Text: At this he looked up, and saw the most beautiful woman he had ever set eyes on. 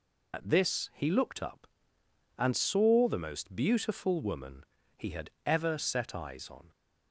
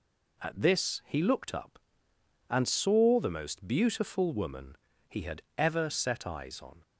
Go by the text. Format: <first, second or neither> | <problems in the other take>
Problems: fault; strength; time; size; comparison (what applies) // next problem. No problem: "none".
second | loses the start of "At"; at 0.3 s; 55 ms // pauses between "woman" and "he"; slight; at 4.6 s; 0.34 s long; slight in the second // pauses between "had" and "ever"; slight; at 5.3 s; 0.16 s long; slight in the second